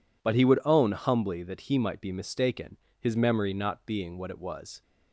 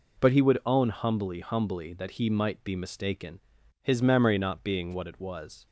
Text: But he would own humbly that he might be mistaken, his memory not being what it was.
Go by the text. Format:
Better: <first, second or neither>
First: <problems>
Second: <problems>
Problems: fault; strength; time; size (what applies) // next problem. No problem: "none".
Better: first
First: none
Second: says "humbly" twice; at 1.3 s